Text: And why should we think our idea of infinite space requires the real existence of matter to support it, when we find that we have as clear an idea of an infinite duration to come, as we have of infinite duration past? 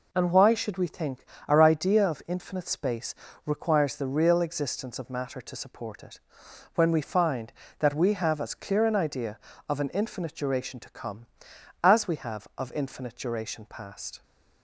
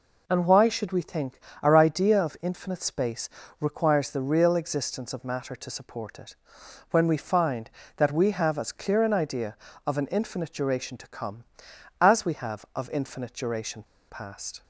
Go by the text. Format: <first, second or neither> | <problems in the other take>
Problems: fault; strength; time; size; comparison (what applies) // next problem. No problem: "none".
first | pauses between "think" and "our"; slight; at 1.3 s; 0.24 s long; slight in the first // pauses between "space" and "requires"; slight; at 3.2 s; 0.30 s long; slight in the first // pauses between "duration" and "past"; slight; at 13.8 s; 0.26 s long